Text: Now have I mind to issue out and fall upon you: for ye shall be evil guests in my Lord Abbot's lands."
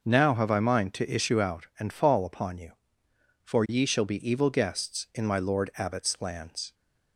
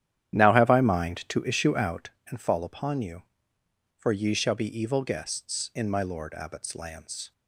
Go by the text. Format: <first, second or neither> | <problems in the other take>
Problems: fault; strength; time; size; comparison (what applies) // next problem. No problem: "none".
first | starts louder than the rest; strong; until 2.1 s; 11 dB